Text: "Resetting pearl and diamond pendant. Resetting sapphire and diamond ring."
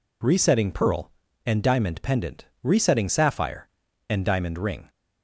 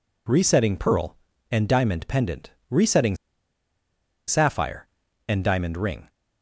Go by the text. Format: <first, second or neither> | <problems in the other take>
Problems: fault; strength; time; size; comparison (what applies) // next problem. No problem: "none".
first | pauses between "Resetting" and "sapphire"; at 3.1 s; 1.1 s long